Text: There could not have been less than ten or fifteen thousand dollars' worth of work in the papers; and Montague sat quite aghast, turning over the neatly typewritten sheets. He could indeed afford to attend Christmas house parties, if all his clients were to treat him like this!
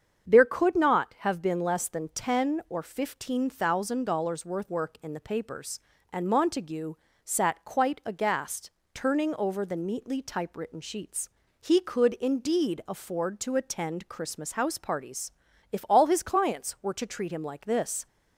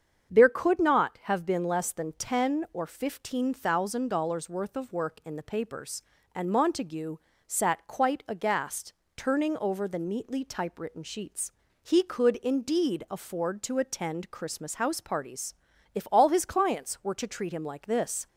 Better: second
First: starts louder than the rest; strong; until 1.3 s; 7 dB // skips "of"; at 4.6 s // pauses between "Montague" and "sat"; slight; at 6.9 s; 0.32 s long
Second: starts louder than the rest; strong; until 1.3 s; 7.5 dB // pauses between "Montague" and "sat"; slight; at 7.1 s; 0.32 s long

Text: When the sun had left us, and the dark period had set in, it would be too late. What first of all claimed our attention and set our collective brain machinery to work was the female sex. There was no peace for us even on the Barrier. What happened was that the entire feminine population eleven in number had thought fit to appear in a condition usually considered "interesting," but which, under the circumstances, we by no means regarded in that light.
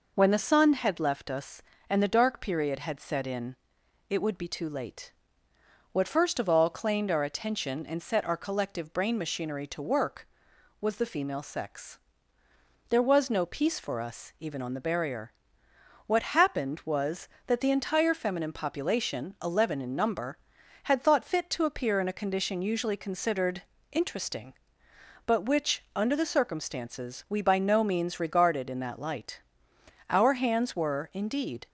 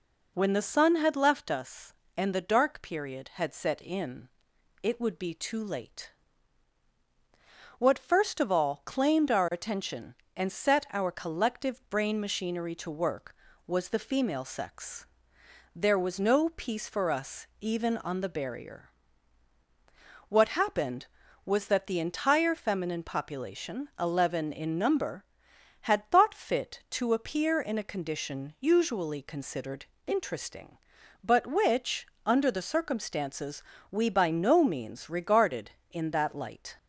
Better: second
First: pauses between "considered" and "interesting"; slight; at 23.6 s; 0.30 s long // goes on to say "Our hands were indeed"; from 30.0 s on; 1.6 s long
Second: pauses between "considered" and "interesting"; slight; at 29.8 s; 0.22 s long

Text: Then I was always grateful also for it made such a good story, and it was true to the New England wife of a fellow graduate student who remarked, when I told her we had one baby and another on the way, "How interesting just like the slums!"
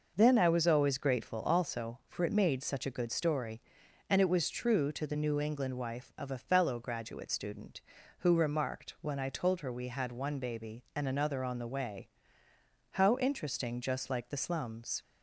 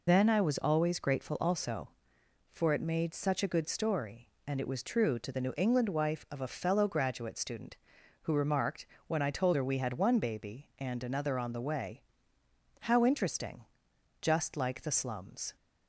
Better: first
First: none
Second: loses the start of "Then"; at 0.0 s; 65 ms // pauses between "interesting" and "just"; noticeable; at 13.6 s; 0.56 s long

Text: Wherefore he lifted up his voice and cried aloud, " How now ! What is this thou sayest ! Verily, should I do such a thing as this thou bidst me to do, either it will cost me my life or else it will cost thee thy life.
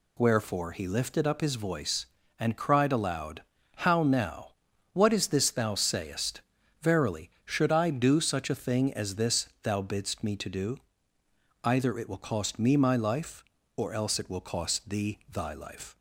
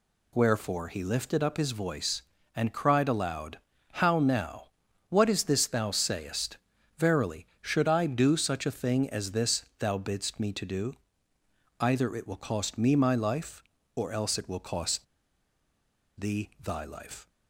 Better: first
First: none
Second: pauses between "cost" and "thee"; at 15.0 s; 1.1 s long

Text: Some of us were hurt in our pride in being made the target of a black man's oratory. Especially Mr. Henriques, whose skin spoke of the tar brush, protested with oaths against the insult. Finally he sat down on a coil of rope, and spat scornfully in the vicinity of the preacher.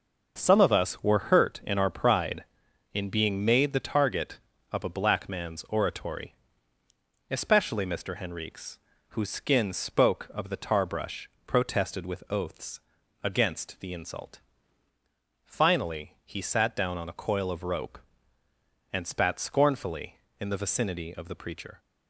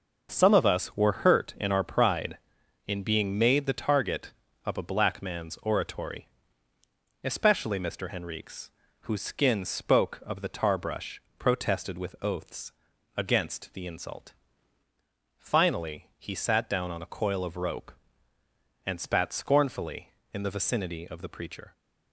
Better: neither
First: pauses between "oaths" and "against"; at 12.8 s; 0.42 s long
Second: pauses between "oaths" and "against"; at 12.7 s; 0.44 s long

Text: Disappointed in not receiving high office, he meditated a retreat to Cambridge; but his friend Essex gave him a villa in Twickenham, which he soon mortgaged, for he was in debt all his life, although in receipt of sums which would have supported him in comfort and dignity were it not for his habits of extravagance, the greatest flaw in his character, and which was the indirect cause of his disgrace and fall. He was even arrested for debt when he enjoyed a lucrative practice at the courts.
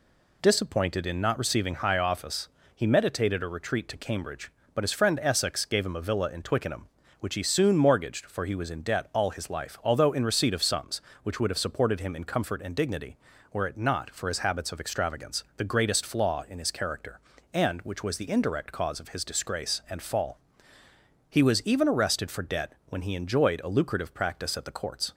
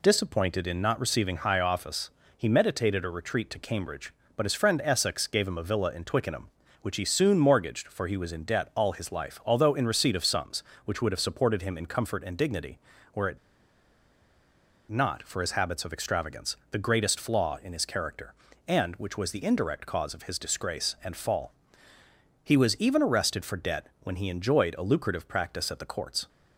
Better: first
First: pauses between "debt" and "when"; slight; at 22.7 s; 0.16 s long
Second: pauses between "it" and "not"; strong; at 13.3 s; 1.5 s long // pauses between "debt" and "when"; slight; at 23.8 s; 0.16 s long

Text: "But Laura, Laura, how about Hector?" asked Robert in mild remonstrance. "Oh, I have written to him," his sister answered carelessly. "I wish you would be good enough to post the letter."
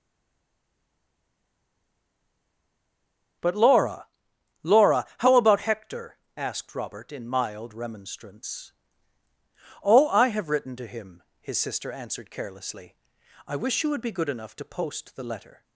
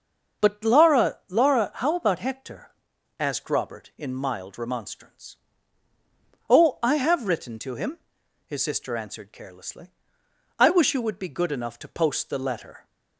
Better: second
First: stays silent before the first word; strong; until 3.4 s; 3.4 s long // starts louder than the rest; strong; until 4.9 s; 7 dB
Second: starts louder than the rest; until 1.5 s; 6.5 dB

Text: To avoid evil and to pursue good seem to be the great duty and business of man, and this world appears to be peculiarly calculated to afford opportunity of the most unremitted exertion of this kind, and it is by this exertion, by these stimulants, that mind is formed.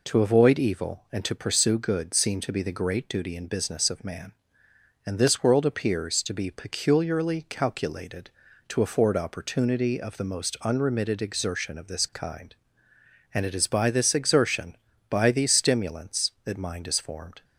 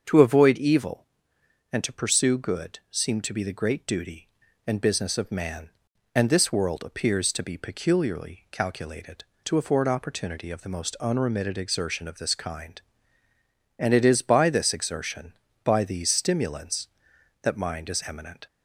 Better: first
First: none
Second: starts louder than the rest; until 1.7 s; 6.5 dB // says "eminent" for "formed"; at 18.0 s

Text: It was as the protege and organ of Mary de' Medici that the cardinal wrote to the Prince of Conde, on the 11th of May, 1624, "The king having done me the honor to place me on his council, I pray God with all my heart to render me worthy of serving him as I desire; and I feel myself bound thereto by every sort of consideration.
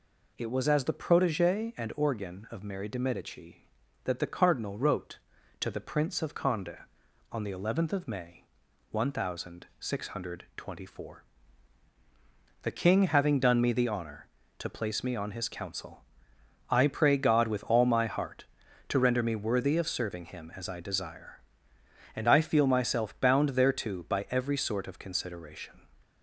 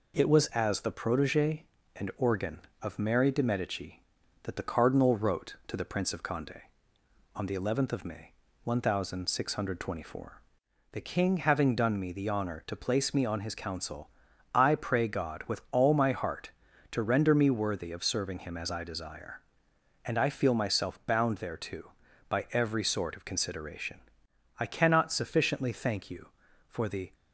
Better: first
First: none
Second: goes on to say "I cannot sufficiently thank you for the"; strong; from 24.6 s on; 2.5 s long

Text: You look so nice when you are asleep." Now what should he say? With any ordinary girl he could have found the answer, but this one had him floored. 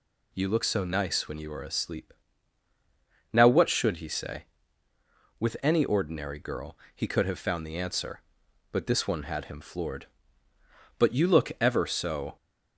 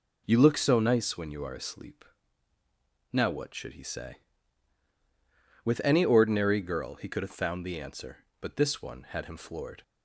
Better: second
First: pauses between "girl" and "he"; slight; at 6.7 s; 0.18 s long // goes on to say "But you look ever so"; from 10.9 s on; 1.3 s long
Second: none

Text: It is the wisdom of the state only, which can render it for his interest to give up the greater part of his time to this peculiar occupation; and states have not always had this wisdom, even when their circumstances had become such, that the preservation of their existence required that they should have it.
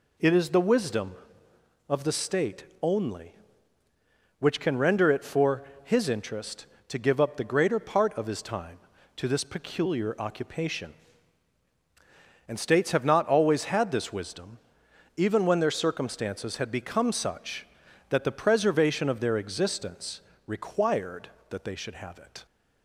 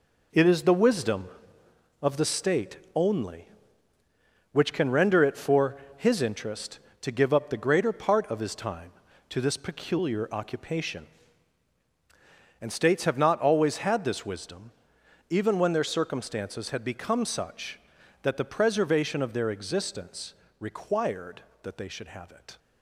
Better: first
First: pauses between "state" and "only"; slight; at 2.6 s; 0.18 s long // pauses between "for" and "his"; slight; at 5.6 s; 0.20 s long // pauses between "existence" and "required"; slight; at 20.1 s; 0.26 s long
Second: gets quieter; strong; throughout; 8 dB // pauses between "state" and "only"; slight; at 2.7 s; 0.18 s long // pauses between "for" and "his"; slight; at 5.7 s; 0.20 s long // pauses between "existence" and "required"; slight; at 20.3 s; 0.26 s long

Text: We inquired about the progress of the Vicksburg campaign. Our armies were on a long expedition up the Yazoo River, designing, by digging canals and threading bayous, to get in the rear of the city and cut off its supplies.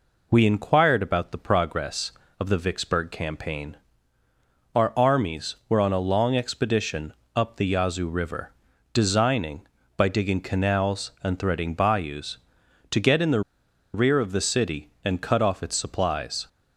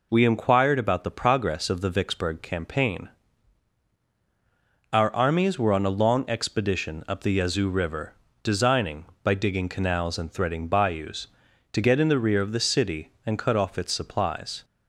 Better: second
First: pauses between "expedition" and "up"; slight; at 7.1 s; 0.22 s long // pauses between "the" and "rear"; noticeable; at 13.4 s; 0.52 s long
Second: none

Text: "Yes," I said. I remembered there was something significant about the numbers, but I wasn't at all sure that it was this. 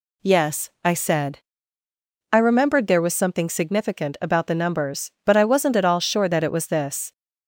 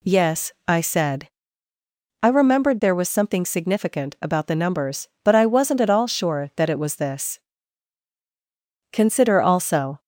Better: first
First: none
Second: goes on to say "Consider also"; noticeable; from 8.9 s on; 1.0 s long

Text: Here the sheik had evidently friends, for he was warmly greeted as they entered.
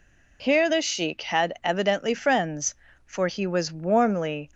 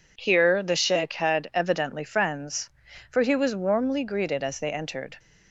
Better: second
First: stops before "greeted as they entered"; at 4.5 s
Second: none

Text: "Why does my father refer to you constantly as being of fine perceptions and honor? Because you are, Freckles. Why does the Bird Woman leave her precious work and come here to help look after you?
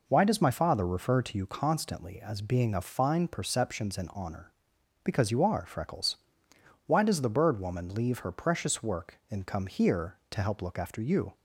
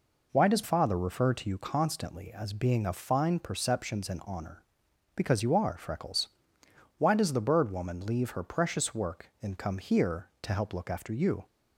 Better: first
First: none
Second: skips "my"; at 0.6 s

